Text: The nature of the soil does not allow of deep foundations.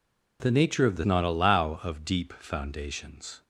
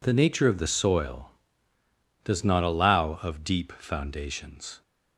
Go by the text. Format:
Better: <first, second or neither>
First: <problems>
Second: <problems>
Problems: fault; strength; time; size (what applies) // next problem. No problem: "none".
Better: second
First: skips "soil does"; at 1.0 s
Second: none